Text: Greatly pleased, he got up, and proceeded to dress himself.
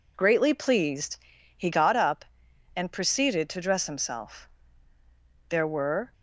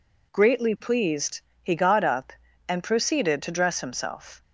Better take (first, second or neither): second